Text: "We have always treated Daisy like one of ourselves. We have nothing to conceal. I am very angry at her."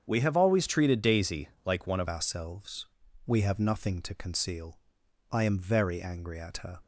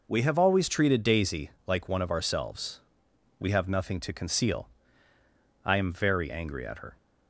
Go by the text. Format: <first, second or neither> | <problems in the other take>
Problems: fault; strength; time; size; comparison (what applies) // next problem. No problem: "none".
second | starts louder than the rest; strong; until 1.0 s; 7.5 dB // pauses between "Daisy" and "like"; slight; at 1.4 s; 0.18 s long; slight in the second // changes voice at "ourselves"; from 2.0 s on; 4.7 s long